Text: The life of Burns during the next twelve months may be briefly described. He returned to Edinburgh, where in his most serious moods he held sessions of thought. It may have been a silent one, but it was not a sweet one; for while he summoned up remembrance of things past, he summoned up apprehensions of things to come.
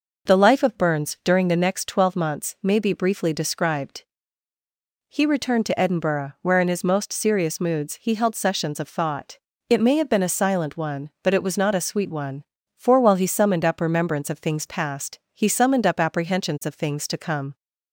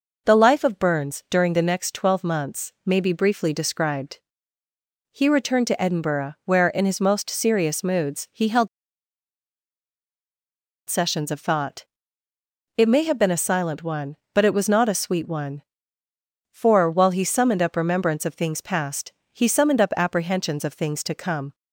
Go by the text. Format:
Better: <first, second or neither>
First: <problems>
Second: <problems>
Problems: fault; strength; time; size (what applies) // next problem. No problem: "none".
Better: first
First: none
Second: pauses between "held" and "sessions"; strong; at 8.6 s; 2.2 s long